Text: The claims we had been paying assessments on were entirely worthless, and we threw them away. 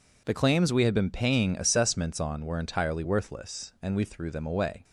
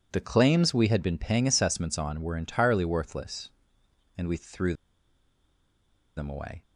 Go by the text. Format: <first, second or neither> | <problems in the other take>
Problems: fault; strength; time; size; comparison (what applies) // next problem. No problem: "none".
first | pauses between "threw" and "them"; strong; at 4.7 s; 1.4 s long